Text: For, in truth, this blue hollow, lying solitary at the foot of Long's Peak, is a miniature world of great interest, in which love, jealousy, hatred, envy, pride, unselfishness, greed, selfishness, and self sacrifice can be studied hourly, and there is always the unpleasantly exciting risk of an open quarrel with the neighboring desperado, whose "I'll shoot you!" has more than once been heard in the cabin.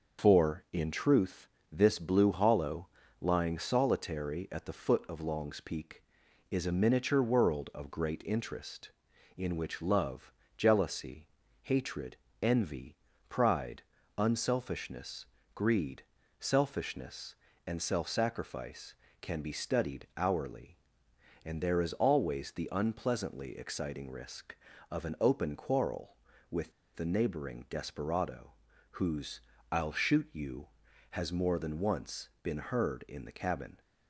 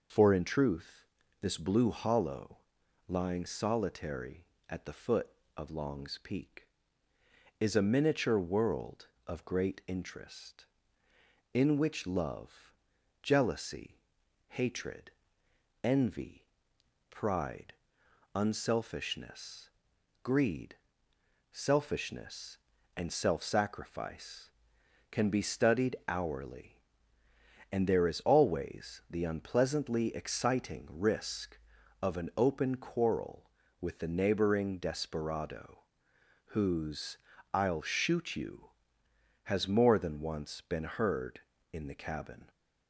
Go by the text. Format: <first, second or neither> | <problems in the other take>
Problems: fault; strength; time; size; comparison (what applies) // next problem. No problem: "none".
second | starts louder than the rest; until 1.2 s; 6 dB // pauses between "with" and "the"; slight; at 26.7 s; 0.23 s long // pauses between "whose" and "I'll"; slight; at 29.3 s; 0.34 s long; slight in the second // pauses between "once" and "been"; slight; at 32.2 s; 0.16 s long